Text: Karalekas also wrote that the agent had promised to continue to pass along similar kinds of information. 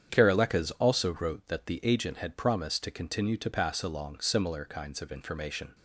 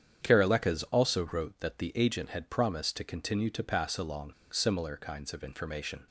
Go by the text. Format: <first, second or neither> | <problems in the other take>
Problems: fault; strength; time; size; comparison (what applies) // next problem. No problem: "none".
first | starts louder than the rest; strong; until 1.3 s; 8.5 dB; strong in the first // pauses between "along" and "similar"; slight; at 4.3 s; 0.18 s long